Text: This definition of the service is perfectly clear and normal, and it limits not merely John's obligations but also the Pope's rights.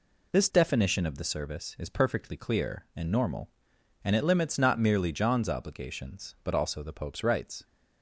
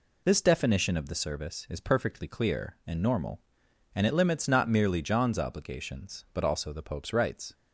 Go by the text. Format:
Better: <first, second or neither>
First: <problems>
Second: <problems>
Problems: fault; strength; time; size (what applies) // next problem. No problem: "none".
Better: neither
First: none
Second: none